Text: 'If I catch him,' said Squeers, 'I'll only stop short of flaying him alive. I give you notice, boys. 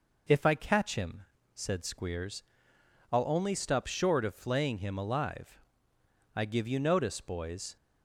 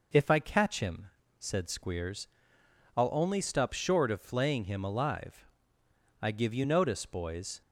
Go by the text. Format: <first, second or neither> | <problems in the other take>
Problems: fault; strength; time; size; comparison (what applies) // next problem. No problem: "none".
neither | none